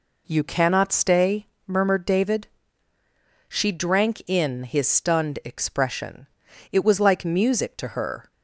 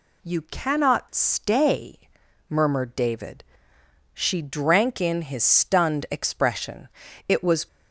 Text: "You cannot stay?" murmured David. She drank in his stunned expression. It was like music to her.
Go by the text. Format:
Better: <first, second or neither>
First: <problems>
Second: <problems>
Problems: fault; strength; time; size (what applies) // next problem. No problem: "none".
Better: first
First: none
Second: stops before "like music to her"; at 7.6 s